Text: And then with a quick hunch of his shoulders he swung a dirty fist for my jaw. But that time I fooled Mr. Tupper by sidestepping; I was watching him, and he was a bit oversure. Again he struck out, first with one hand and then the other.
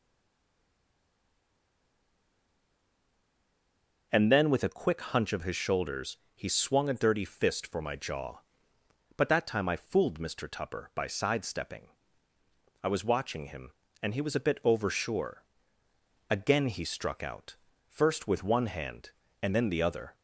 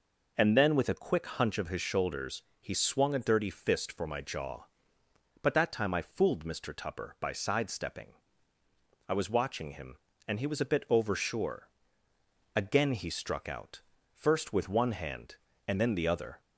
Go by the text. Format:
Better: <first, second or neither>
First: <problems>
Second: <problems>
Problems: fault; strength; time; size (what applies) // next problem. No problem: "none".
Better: second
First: stays silent before the first word; strong; until 4.1 s; 4.1 s long // pauses between "shoulders" and "he"; slight; at 6.1 s; 0.18 s long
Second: pauses between "shoulders" and "he"; slight; at 2.4 s; 0.18 s long